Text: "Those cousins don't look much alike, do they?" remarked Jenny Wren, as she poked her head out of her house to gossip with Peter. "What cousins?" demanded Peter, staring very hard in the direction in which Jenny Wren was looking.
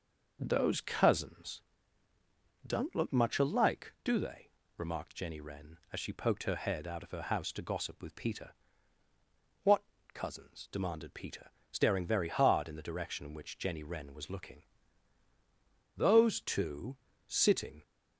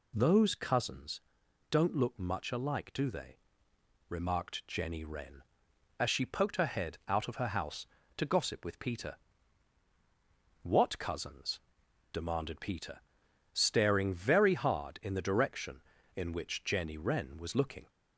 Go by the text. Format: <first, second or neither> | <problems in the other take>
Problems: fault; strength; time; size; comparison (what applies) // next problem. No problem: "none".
second | pauses between "cousins" and "don't"; at 1.6 s; 1.0 s long; noticeable in the second // pauses between "What" and "cousins"; slight; at 9.8 s; 0.30 s long // goes on to say "Those two sitting"; strong; from 15.9 s on; 1.8 s long